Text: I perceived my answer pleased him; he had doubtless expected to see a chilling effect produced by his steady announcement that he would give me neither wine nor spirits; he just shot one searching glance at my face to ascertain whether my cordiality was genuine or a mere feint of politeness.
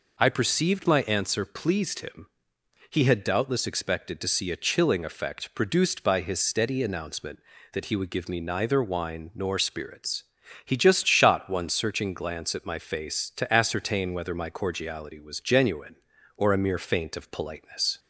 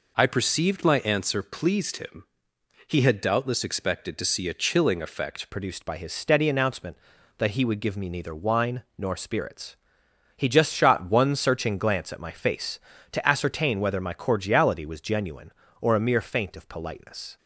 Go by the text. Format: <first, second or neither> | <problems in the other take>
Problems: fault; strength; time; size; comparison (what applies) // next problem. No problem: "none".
first | changes voice at "produced"; from 5.4 s on; 11.9 s long